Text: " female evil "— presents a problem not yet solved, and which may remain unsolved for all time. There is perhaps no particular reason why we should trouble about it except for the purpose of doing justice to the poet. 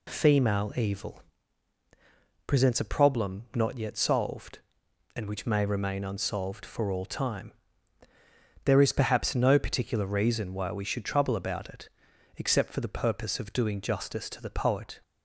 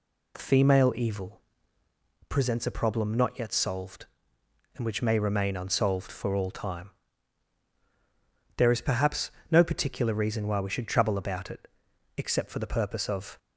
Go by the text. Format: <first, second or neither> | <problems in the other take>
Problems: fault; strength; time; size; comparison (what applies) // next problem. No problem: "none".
first | pauses between "perhaps" and "no"; slight; at 9.2 s; 0.20 s long // pauses between "it" and "except"; noticeable; at 11.6 s; 0.52 s long; noticeable in the first // stops before "doing justice to the poet"; at 13.3 s